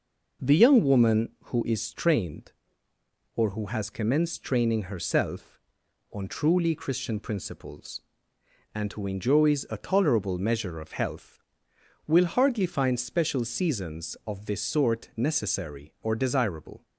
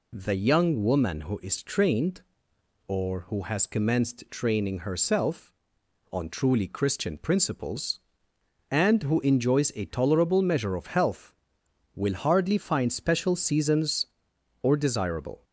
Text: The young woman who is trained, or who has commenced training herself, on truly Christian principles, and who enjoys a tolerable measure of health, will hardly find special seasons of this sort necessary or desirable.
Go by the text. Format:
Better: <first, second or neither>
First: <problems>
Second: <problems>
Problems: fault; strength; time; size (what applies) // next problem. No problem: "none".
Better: first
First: none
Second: skips "of this sort necessary"; at 14.3 s